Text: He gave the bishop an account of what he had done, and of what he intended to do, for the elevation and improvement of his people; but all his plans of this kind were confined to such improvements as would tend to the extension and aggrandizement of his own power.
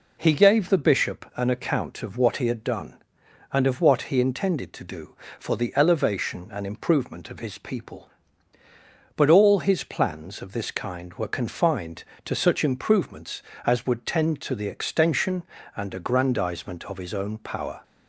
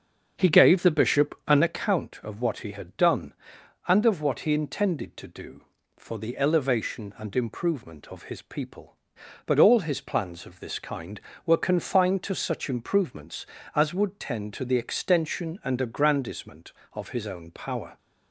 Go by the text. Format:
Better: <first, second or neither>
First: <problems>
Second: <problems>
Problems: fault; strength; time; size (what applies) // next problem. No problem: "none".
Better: first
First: none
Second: starts louder than the rest; until 1.8 s; 6.5 dB